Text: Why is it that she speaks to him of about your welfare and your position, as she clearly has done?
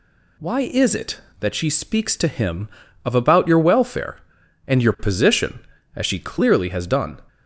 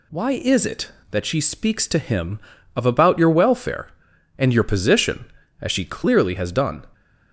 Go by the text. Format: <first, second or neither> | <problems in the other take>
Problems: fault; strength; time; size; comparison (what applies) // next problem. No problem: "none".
neither | none